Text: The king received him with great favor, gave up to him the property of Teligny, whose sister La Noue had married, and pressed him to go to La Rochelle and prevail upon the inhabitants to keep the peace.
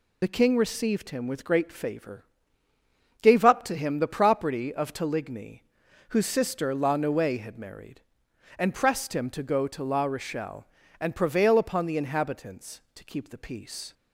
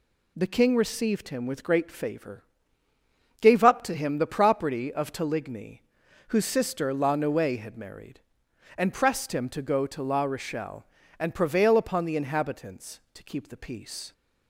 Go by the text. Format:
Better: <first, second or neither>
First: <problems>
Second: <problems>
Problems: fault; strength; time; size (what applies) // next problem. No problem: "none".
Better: second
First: loses the start of "The"; at 0.2 s; 50 ms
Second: none